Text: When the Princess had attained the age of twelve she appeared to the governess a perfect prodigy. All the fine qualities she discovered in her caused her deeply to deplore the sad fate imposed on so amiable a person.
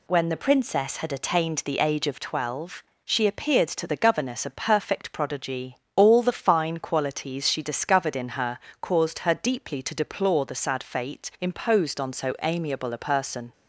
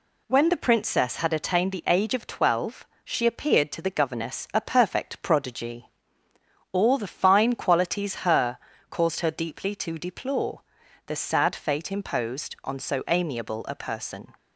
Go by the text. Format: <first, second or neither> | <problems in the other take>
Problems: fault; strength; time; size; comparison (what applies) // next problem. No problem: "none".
first | pauses between "twelve" and "she"; slight; at 2.8 s; 0.18 s long; slight in the first // skips "she discovered in"; at 8.2 s // pauses between "her" and "caused"; slight; at 8.5 s; 0.32 s long; slight in the first // pauses between "deplore" and "the"; at 10.6 s; 0.44 s long